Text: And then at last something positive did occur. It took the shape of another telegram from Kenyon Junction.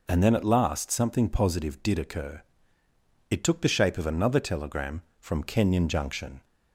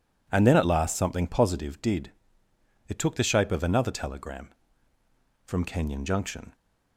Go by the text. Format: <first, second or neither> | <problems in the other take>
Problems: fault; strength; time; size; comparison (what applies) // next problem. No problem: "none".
first | skips "occur"; at 2.4 s